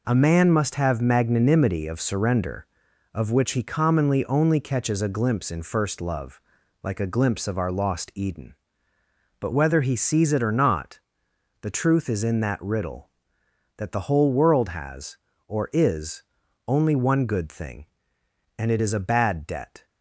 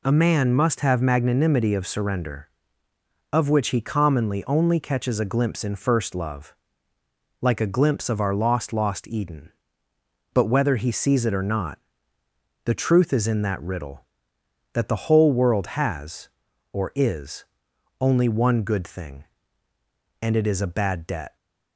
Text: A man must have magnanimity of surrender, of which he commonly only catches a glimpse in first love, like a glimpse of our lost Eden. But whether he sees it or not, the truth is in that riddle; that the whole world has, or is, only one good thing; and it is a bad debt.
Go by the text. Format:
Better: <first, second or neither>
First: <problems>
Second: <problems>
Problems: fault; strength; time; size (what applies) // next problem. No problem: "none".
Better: first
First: none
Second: says "lost" twice; at 8.7 s